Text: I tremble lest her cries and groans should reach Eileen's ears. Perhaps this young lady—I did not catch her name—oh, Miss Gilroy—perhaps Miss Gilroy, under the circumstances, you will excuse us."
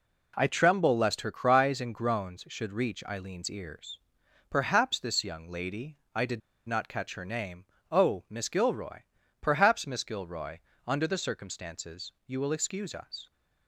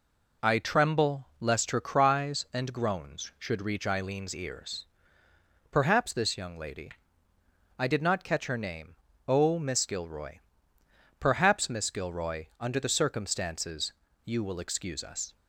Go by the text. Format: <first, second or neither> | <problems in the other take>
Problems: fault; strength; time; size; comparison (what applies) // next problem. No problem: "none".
second | pauses between "did" and "not"; slight; at 6.4 s; 0.28 s long